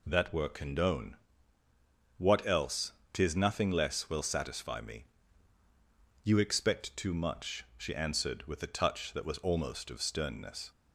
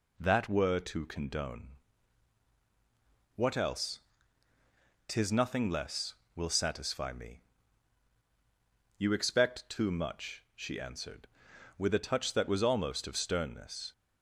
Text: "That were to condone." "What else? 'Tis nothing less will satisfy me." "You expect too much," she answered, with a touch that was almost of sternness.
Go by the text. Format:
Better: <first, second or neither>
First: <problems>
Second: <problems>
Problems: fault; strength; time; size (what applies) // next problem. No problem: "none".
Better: second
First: skips "to"; at 0.4 s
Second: none